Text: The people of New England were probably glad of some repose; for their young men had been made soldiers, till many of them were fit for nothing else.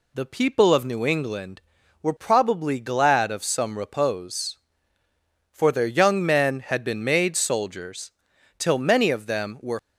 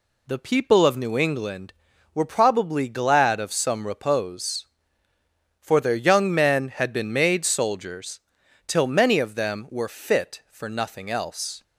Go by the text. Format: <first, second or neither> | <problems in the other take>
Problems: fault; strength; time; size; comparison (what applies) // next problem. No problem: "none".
second | stops before "fit for nothing else"; at 9.7 s